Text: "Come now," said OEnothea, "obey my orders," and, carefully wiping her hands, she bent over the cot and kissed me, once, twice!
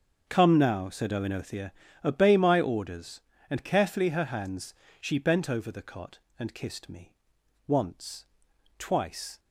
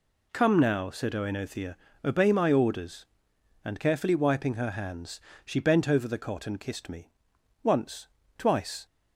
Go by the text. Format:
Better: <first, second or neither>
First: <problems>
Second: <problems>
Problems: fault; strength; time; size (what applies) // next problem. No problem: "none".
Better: second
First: starts louder than the rest; until 1.2 s; 6.5 dB // skips "wiping"; at 4.0 s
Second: none